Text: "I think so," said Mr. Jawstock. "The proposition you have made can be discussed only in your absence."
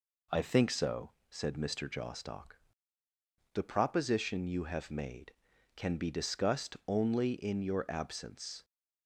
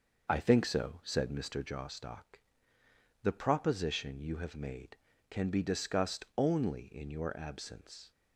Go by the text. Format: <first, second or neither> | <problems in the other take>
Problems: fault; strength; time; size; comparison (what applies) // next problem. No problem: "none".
first | starts louder than the rest; noticeable; until 1.8 s; 5.5 dB